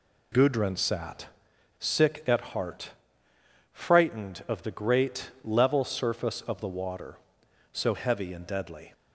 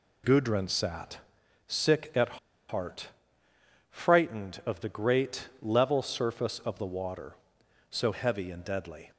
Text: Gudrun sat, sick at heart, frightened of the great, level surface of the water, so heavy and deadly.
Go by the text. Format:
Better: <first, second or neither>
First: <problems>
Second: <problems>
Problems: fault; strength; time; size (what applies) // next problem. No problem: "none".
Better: first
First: none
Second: pauses between "at" and "heart"; slight; at 2.3 s; 0.31 s long